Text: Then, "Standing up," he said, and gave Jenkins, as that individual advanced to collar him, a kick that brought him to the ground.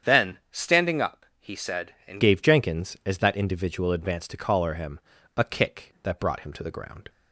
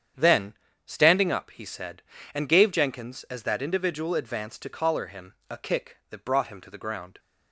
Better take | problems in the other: second | starts louder than the rest; strong; until 1.1 s; 8 dB; strong in the second // changes voice at "gave"; from 2.2 s on; 4.8 s long

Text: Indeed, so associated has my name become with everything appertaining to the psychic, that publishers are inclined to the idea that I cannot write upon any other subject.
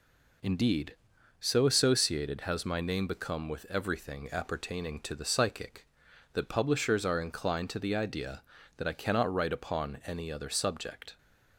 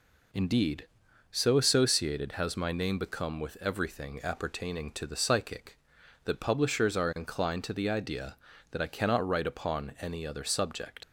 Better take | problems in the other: first | leaves "subject" unfinished; at 11.0 s; 85 ms

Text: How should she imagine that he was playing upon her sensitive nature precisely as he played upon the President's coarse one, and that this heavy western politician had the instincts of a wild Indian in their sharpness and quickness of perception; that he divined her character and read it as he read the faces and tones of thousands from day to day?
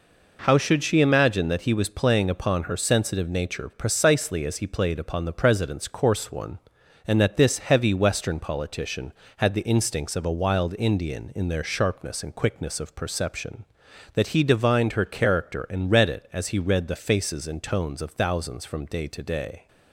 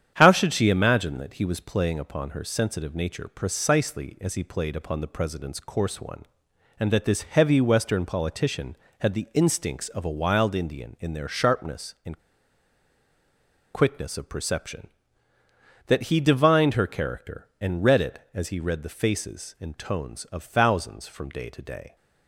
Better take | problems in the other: first | starts louder than the rest; strong; until 1.1 s; 9 dB // pauses between "and" and "quickness"; strong; at 12.2 s; 1.5 s long

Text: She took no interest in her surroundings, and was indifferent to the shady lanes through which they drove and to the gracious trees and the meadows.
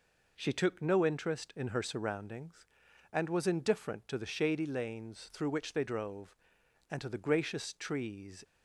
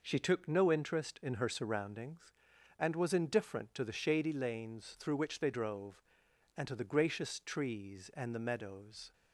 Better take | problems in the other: second | stops before "and the meadows"; at 8.4 s

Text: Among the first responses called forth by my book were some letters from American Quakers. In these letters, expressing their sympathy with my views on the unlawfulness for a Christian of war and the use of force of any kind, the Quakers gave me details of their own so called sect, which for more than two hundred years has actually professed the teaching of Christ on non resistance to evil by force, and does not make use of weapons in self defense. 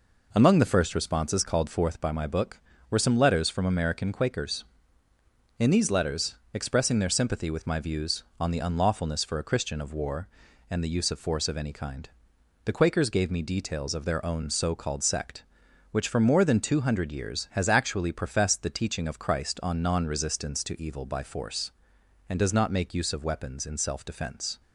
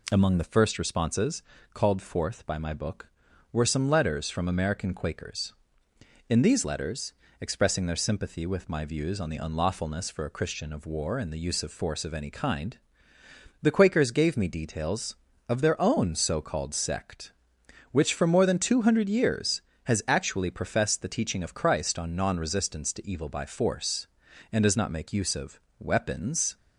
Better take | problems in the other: first | pauses between "responses" and "called"; slight; at 1.4 s; 0.32 s long // pauses between "of" and "weapons"; slight; at 25.6 s; 0.18 s long // stops before "in self defense"; at 26.5 s

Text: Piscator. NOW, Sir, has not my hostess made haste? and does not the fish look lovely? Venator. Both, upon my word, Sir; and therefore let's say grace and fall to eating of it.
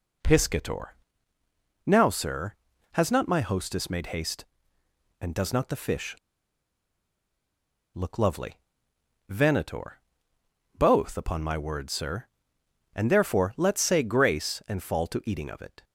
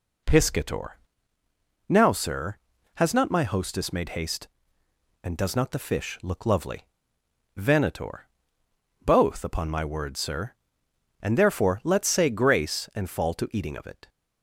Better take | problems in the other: second | pauses between "fish" and "look"; strong; at 6.1 s; 1.7 s long

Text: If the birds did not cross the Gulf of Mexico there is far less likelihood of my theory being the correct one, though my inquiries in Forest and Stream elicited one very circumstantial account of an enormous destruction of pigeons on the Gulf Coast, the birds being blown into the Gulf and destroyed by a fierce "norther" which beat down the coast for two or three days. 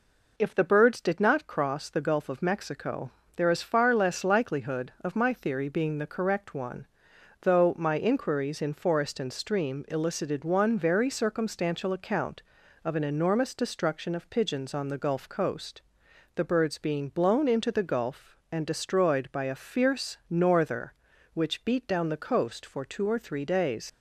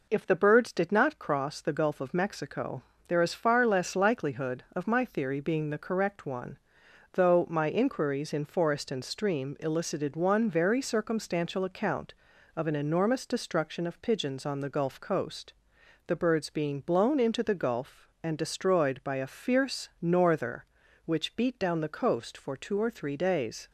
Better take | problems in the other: second | pauses between "Mexico" and "there"; slight; at 3.1 s; 0.26 s long; slight in the second // leaves "days" unfinished; at 23.8 s; 85 ms

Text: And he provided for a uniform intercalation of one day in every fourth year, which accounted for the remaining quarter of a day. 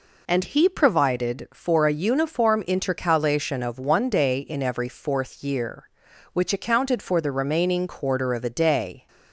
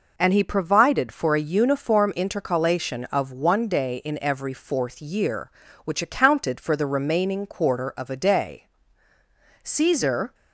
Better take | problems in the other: first | goes on to say "Caesar"; noticeable; from 9.6 s on; 0.70 s long

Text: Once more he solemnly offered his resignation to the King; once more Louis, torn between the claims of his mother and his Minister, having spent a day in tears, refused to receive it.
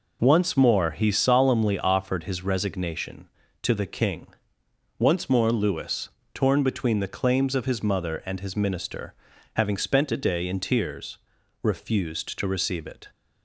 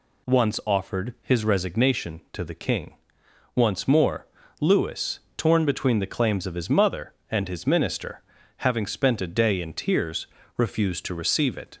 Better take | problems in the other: first | skips "more he solemnly"; at 0.6 s // pauses between "more" and "Louis"; slight; at 4.2 s; 0.32 s long

